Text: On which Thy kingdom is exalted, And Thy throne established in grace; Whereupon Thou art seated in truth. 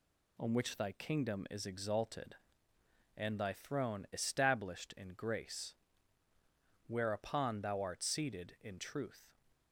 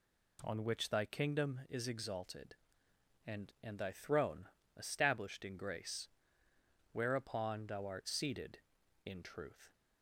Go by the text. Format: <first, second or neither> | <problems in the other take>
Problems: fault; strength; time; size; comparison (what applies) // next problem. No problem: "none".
first | says "And" twice; at 3.6 s // pauses between "throne" and "established"; slight; at 4.4 s; 0.30 s long